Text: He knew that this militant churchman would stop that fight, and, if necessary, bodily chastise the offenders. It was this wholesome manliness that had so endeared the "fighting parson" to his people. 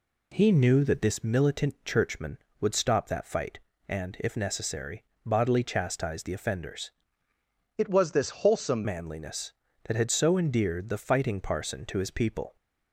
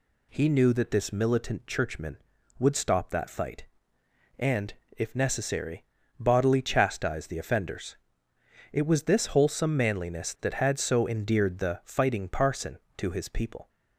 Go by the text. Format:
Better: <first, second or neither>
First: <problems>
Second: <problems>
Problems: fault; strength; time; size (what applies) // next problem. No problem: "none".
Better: second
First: changes voice from "It" to "wholesome"; from 7.7 to 8.8 s; 1.1 s long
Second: none